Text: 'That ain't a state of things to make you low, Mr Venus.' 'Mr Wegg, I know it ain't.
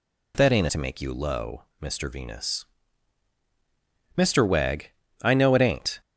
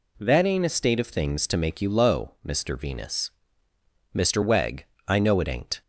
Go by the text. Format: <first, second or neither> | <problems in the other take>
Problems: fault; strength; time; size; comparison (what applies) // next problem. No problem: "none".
second | skips "a state of things"; at 0.6 s